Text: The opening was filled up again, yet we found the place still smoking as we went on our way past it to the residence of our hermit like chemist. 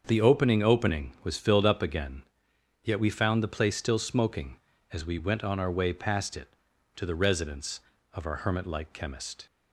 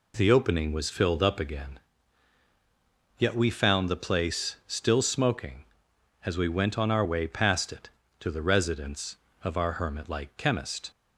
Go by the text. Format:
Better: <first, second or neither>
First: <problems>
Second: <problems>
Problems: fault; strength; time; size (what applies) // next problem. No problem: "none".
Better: second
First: starts louder than the rest; until 1.0 s; 6.5 dB // says "opening" twice; at 0.6 s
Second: none